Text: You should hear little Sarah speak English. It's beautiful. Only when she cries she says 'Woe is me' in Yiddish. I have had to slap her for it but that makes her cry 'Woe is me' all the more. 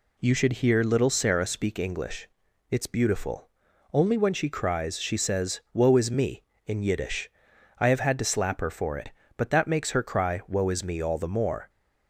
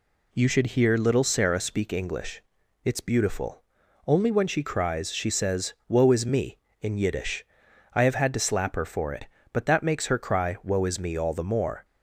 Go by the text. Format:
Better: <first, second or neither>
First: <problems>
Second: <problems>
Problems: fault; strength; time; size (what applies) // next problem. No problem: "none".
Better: neither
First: none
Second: none